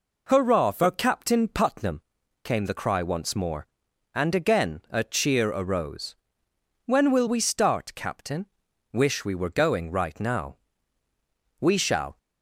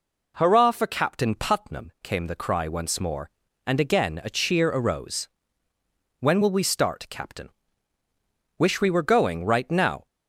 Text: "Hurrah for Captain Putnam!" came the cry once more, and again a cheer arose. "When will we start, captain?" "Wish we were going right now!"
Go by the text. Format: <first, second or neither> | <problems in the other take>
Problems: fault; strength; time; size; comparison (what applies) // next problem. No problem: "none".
second | goes on to say "We shall"; from 11.5 s on; 0.58 s long